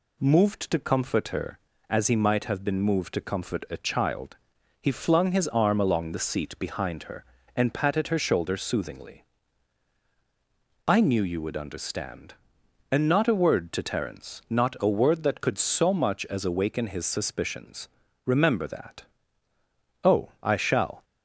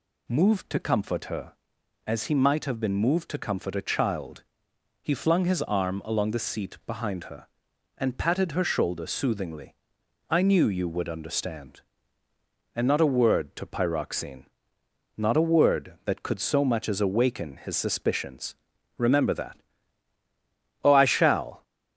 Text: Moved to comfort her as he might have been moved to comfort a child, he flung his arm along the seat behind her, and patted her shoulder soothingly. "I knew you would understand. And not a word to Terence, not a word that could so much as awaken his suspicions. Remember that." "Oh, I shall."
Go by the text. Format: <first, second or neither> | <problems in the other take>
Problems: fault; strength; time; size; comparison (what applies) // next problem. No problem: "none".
first | says "Pyroxene" for "Terence"; at 13.6 s